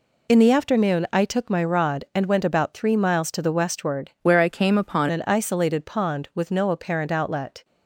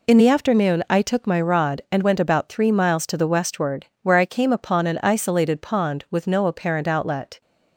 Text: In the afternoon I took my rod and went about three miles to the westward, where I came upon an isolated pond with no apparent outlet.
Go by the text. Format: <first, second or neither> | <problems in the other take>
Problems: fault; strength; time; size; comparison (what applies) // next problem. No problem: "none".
second | changes voice from "where" to "upon"; from 4.2 to 5.0 s; 0.8 s long